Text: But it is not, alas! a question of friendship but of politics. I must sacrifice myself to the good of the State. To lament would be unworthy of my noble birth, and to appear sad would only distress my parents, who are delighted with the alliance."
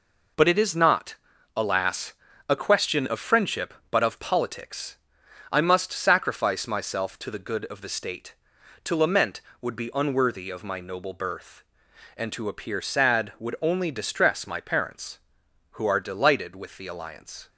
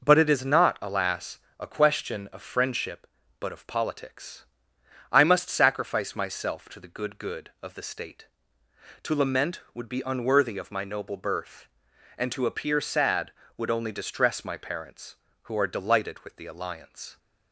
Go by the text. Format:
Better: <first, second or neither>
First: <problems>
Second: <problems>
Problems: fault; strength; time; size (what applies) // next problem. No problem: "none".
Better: first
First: none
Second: says "good" twice; at 7.1 s